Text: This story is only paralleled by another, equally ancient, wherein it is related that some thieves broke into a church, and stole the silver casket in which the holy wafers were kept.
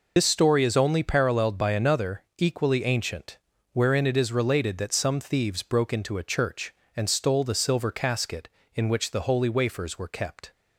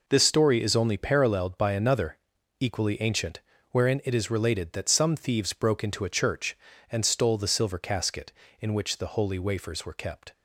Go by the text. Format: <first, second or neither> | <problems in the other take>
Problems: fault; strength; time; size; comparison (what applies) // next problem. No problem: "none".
second | loses the start of "This"; at 0.1 s; 45 ms